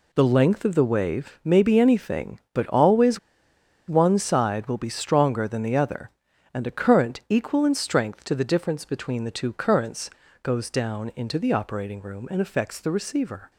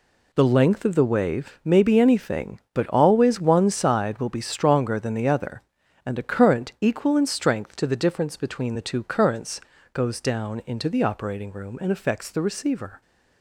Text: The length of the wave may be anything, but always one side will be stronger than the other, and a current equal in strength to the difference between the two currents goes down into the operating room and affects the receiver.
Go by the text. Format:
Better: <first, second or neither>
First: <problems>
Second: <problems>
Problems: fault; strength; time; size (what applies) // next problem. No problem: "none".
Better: second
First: pauses between "always" and "one"; noticeable; at 3.1 s; 0.70 s long // pauses between "currents" and "goes"; slight; at 10.0 s; 0.34 s long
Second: pauses between "currents" and "goes"; slight; at 9.5 s; 0.34 s long